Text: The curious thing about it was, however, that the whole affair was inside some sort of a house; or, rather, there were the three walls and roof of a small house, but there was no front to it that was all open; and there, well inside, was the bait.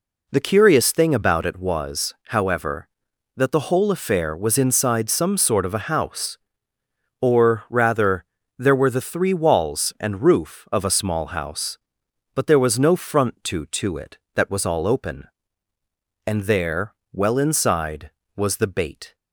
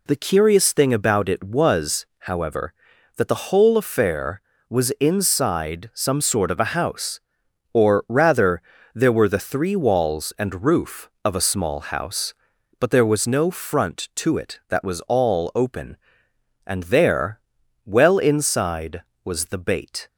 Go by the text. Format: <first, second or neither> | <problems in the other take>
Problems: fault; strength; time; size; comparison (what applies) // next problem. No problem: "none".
second | says "to" twice; at 13.6 s